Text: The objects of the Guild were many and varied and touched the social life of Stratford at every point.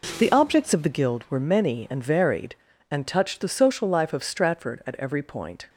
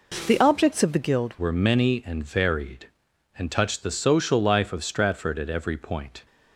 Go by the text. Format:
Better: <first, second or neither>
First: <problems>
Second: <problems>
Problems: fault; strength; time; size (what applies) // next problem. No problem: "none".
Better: first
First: none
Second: changes voice at "were"; from 1.3 s on; 4.9 s long